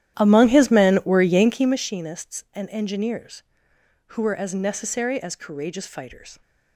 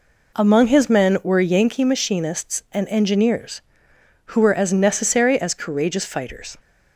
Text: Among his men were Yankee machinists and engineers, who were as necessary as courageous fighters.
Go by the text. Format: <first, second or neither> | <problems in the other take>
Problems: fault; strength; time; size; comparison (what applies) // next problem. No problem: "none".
second | starts louder than the rest; strong; until 2.0 s; 11.5 dB